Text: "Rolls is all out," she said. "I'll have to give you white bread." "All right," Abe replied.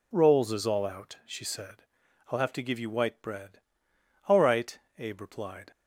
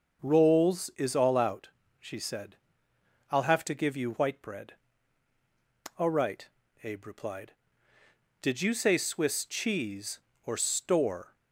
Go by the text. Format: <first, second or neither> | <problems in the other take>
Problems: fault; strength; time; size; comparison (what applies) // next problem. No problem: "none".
first | starts louder than the rest; until 1.3 s; 6 dB // goes on to say "Did you say Swiss cheese or store"; strong; from 8.4 s on; 2.9 s long